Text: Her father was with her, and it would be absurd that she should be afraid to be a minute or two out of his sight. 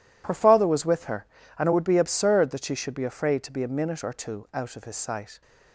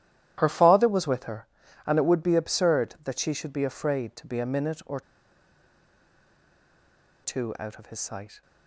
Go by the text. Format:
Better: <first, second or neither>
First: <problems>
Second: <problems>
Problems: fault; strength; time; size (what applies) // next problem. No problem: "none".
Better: first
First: none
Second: starts louder than the rest; strong; until 1.3 s; 12 dB // pauses between "or" and "two"; strong; at 5.0 s; 2.2 s long